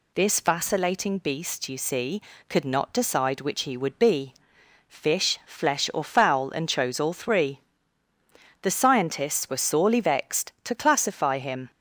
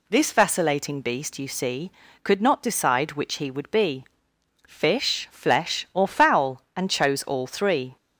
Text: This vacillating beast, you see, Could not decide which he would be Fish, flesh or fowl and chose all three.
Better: second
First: pauses between "be" and "Fish"; noticeable; at 4.3 s; 0.54 s long // goes on to say "The scientists were sorely vexed To classify him"; strong; from 8.6 s on; 3.0 s long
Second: pauses between "be" and "Fish"; noticeable; at 4.0 s; 0.64 s long

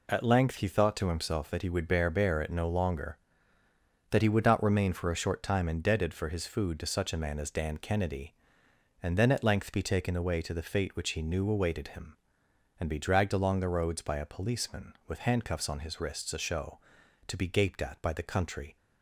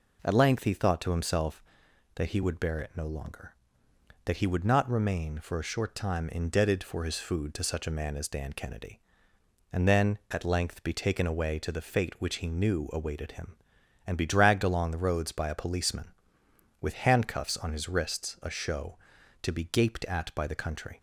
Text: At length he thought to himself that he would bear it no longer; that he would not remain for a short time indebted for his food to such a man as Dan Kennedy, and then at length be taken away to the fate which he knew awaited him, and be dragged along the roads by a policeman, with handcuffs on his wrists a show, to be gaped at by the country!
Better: second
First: says "bear" twice; at 2.1 s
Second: none

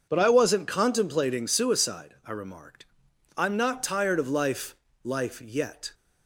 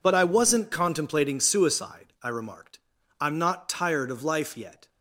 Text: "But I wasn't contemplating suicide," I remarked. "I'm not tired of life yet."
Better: second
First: says "life" twice; at 5.0 s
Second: none

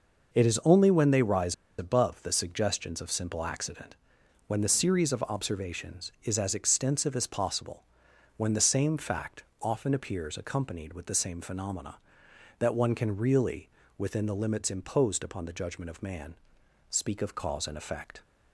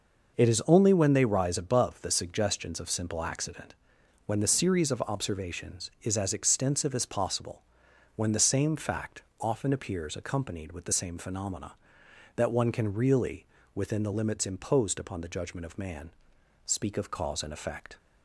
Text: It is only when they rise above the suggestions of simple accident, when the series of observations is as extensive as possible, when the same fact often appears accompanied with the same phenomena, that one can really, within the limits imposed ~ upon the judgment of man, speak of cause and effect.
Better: second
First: starts louder than the rest; noticeable; until 1.3 s; 6 dB // pauses between "rise" and "above"; slight; at 1.5 s; 0.25 s long // pauses between "fact" and "often"; slight; at 9.4 s; 0.18 s long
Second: starts louder than the rest; noticeable; until 1.3 s; 6 dB // pauses between "fact" and "often"; slight; at 9.2 s; 0.18 s long

